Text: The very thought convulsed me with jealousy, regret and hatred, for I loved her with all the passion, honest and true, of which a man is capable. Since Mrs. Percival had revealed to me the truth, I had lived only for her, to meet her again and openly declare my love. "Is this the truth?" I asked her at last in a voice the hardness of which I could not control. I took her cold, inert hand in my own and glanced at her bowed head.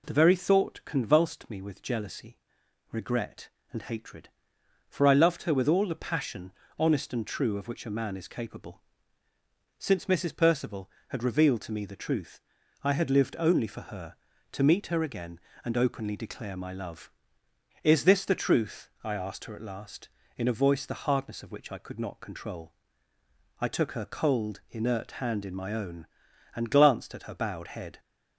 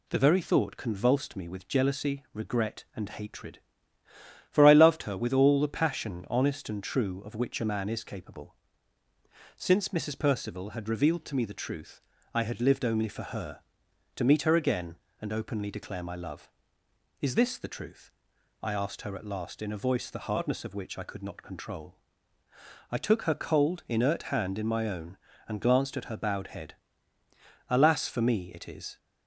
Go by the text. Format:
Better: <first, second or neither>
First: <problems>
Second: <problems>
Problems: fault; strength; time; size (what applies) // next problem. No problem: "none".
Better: first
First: none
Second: goes on to say "Alas for me it is"; noticeable; from 27.7 s on; 1.2 s long